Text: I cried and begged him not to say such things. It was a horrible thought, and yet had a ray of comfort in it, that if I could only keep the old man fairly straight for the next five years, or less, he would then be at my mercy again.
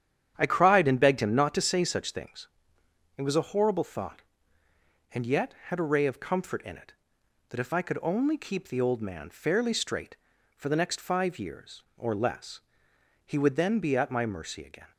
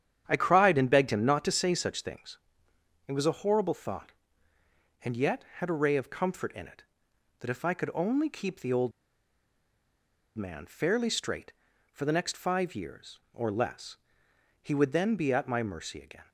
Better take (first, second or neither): first